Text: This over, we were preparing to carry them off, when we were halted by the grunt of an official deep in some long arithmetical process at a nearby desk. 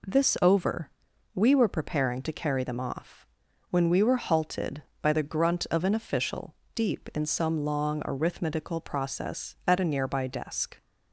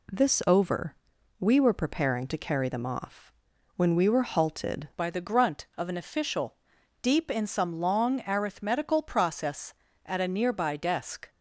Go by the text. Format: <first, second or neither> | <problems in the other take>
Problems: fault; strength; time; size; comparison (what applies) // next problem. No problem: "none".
first | changes voice at "by"; from 4.9 s on; 6.3 s long // pauses between "official" and "deep"; noticeable; at 6.5 s; 0.48 s long; slight in the first